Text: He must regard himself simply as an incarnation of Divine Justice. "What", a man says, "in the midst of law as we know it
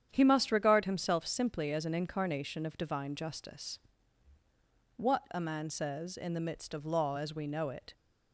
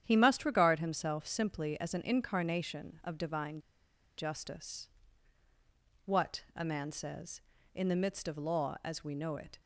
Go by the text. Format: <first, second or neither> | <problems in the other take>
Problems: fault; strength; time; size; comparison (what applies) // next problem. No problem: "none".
first | starts louder than the rest; strong; until 1.0 s; 9.5 dB; strong in the first // pauses between "Divine" and "Justice"; noticeable; at 3.6 s; 0.56 s long